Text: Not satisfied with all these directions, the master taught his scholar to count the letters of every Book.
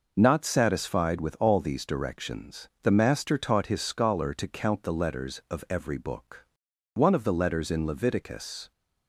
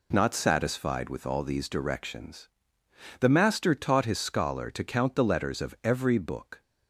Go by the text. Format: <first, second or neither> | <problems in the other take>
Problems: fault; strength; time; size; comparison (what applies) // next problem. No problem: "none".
second | goes on to say "One of the letters in Leviticus"; strong; from 6.9 s on; 1.7 s long